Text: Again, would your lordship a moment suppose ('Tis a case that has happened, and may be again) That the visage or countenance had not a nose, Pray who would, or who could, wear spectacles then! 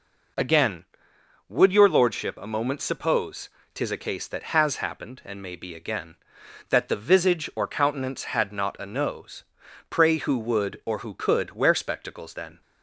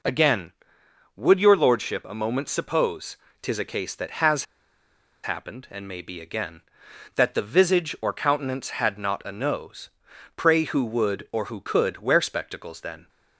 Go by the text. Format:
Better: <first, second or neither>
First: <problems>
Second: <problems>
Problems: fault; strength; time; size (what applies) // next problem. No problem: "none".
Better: first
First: none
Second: pauses between "has" and "happened"; noticeable; at 4.4 s; 0.79 s long